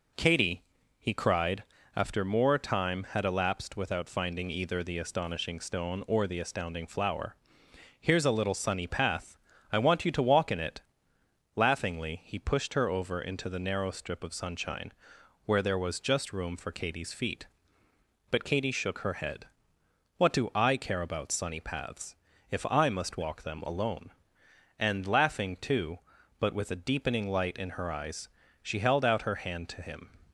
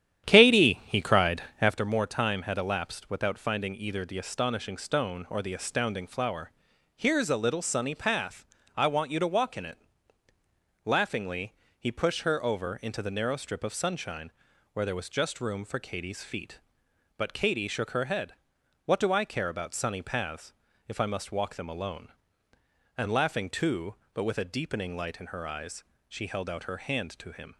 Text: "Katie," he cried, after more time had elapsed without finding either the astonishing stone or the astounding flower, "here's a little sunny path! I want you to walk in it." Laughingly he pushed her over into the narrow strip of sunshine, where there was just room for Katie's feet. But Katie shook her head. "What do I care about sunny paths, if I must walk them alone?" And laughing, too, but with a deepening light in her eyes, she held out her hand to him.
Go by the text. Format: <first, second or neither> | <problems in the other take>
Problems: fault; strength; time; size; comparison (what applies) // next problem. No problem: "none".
first | starts louder than the rest; strong; until 1.8 s; 10.5 dB // pauses between "Laughingly" and "he"; slight; at 11.5 s; 0.24 s long